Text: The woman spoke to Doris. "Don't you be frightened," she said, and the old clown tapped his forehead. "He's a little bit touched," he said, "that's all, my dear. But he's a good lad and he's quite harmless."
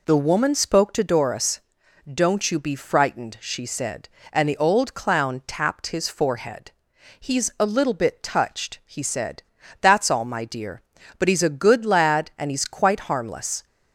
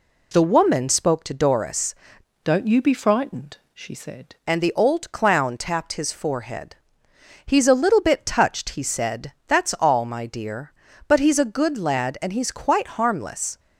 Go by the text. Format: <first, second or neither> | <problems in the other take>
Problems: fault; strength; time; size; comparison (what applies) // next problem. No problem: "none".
first | changes voice from "Don't" to "said"; from 2.4 to 4.3 s; 1.9 s long